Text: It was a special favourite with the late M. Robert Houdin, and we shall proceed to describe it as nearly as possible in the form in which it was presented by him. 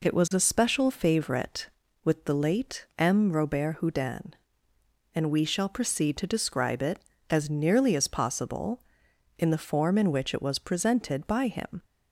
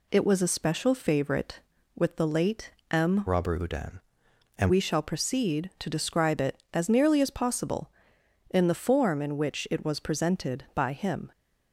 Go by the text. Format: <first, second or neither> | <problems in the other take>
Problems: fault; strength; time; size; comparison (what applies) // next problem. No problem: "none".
first | pauses between "late" and "M"; slight; at 2.6 s; 0.20 s long // changes voice from "Robert" to "and"; from 3.2 to 4.7 s; 1.5 s long